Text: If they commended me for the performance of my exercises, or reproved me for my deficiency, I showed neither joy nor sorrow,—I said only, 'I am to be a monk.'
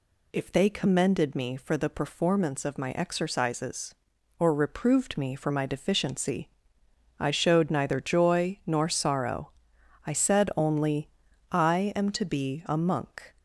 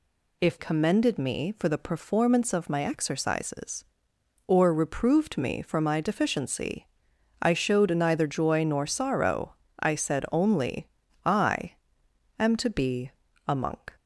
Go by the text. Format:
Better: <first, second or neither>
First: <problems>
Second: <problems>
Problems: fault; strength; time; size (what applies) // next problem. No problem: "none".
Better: first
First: none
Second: skips "they"; at 0.5 s // pauses between "I" and "am"; noticeable; at 11.7 s; 0.66 s long // pauses between "be" and "a"; slight; at 13.1 s; 0.36 s long